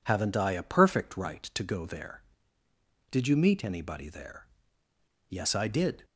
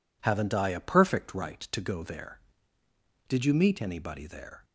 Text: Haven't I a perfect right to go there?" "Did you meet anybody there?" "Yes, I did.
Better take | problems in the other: first | stops before "Yes I did"; at 4.6 s

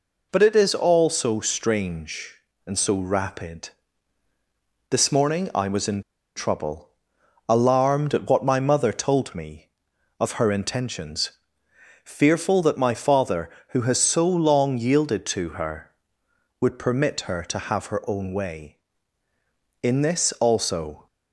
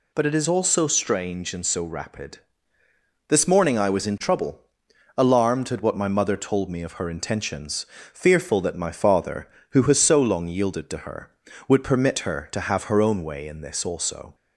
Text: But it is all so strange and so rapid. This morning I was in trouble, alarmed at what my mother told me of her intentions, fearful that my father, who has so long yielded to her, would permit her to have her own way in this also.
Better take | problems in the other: second | pauses between "in" and "trouble"; slight; at 6.0 s; 0.34 s long

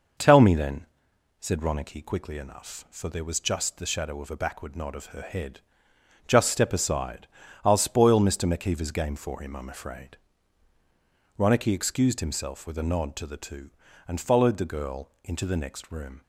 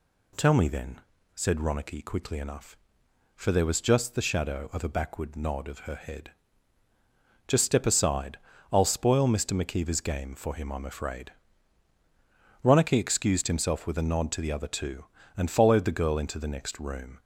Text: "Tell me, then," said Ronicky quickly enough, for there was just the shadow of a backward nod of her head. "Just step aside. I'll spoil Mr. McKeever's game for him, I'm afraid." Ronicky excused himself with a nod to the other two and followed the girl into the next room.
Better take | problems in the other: second | skips "other"; at 13.3 s

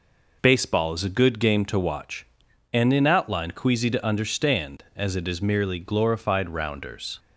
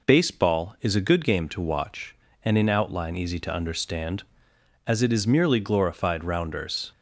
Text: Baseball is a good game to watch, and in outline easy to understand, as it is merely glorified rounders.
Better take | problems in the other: second | says "queasy" for "easy"; at 3.5 s

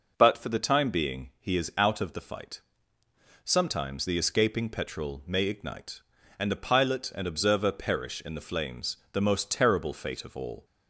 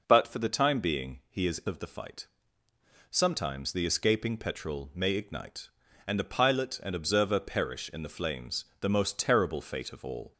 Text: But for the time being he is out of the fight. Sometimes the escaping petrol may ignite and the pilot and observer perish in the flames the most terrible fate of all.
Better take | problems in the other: first | skips "out"; at 1.6 s // pauses between "flames" and "the"; slight; at 8.6 s; 0.16 s long; slight in the first

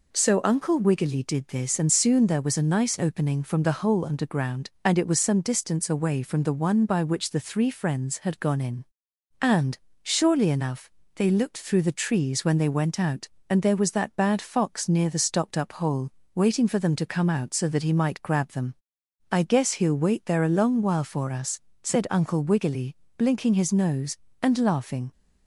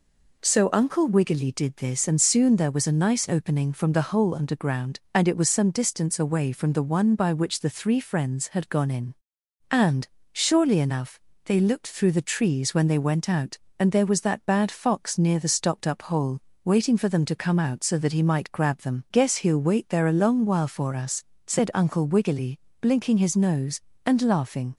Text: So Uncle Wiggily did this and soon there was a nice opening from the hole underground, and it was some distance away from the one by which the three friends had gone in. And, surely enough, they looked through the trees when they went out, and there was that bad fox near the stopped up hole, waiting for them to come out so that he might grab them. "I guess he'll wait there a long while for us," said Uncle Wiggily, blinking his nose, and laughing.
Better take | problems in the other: first | skips "I"; at 19.0 s

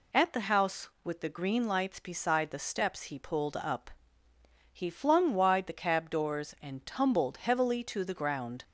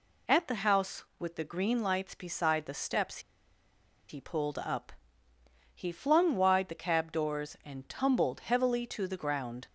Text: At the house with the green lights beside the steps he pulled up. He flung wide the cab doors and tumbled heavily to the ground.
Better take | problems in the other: first | pauses between "steps" and "he"; noticeable; at 3.1 s; 0.89 s long

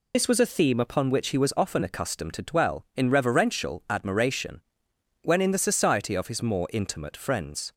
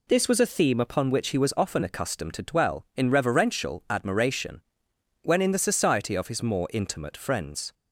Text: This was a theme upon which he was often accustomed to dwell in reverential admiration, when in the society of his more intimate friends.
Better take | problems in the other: second | loses the start of "This"; at 0.1 s; 60 ms

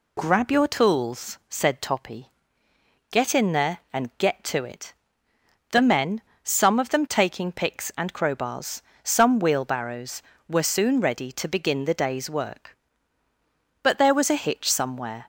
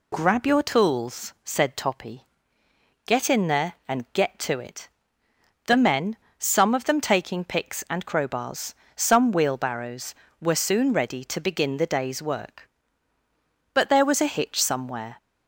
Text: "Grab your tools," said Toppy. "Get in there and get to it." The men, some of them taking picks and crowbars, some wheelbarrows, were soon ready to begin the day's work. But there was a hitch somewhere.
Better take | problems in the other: neither | none

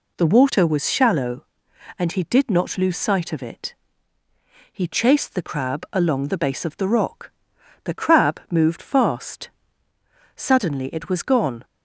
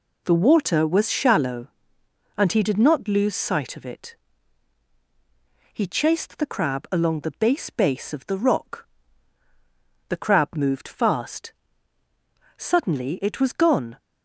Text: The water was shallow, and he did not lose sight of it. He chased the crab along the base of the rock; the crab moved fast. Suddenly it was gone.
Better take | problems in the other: first | says "base" twice; at 7.6 s

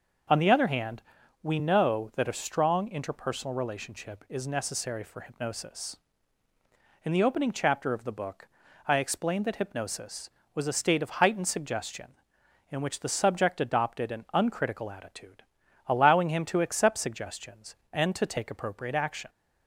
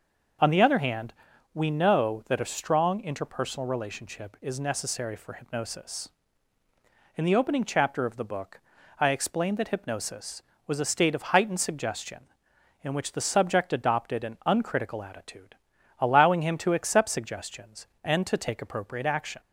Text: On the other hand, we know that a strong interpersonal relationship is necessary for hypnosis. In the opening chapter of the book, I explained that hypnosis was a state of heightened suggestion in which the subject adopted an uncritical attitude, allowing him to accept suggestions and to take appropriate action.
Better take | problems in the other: neither | starts louder than the rest; the same in both

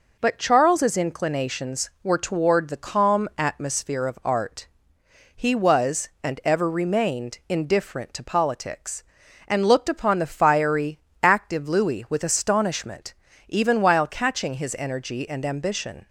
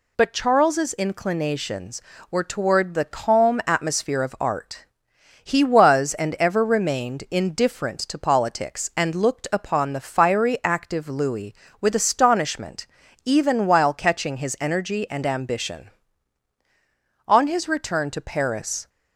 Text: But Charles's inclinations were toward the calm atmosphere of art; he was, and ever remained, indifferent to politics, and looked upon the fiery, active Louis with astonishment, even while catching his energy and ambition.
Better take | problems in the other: first | goes on to say "On his return to Paris"; from 17.2 s on; 1.6 s long

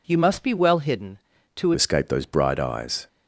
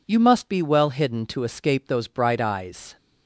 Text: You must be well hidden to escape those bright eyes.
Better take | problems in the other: second | changes voice at "escape"; from 1.7 s on; 1.3 s long

